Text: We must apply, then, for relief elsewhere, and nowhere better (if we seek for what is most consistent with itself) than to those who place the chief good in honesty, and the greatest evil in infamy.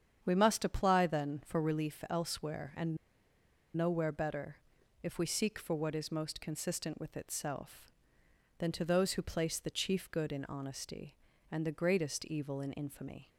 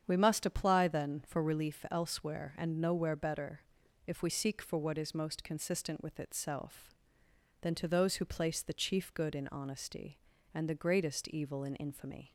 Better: second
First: starts louder than the rest; strong; until 1.2 s; 8 dB // pauses between "and" and "nowhere"; noticeable; at 2.9 s; 0.79 s long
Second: starts louder than the rest; strong; until 1.0 s; 8 dB

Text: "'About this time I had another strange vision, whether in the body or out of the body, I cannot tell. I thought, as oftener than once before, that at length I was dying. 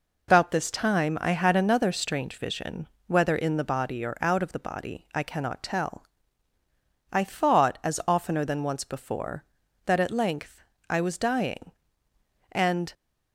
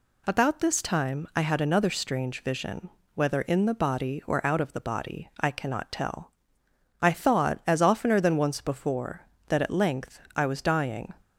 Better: second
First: pauses between "length" and "I"; slight; at 10.6 s; 0.26 s long // goes on to say "And"; slight; from 12.5 s on; 0.42 s long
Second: none

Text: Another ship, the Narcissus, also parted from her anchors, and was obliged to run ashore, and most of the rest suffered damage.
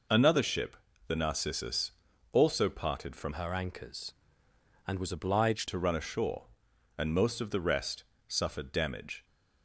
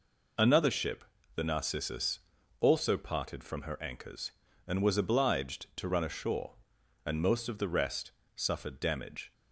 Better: second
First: changes voice from "her" to "obliged"; from 3.3 to 5.6 s; 2.3 s long // pauses between "rest" and "suffered"; slight; at 8.0 s; 0.24 s long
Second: pauses between "rest" and "suffered"; slight; at 8.1 s; 0.24 s long

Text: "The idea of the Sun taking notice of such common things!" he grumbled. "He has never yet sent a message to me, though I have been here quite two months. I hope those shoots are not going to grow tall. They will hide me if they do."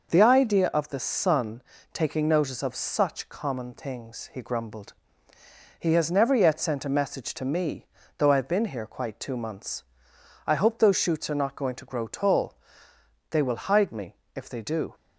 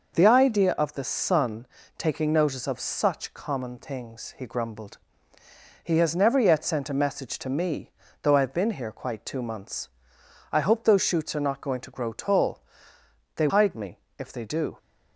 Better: first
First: pauses between "Sun" and "taking"; slight; at 1.6 s; 0.32 s long // pauses between "me" and "if"; slight; at 14.1 s; 0.20 s long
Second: pauses between "Sun" and "taking"; slight; at 1.6 s; 0.32 s long // skips "will"; at 13.4 s // pauses between "me" and "if"; slight; at 13.9 s; 0.20 s long

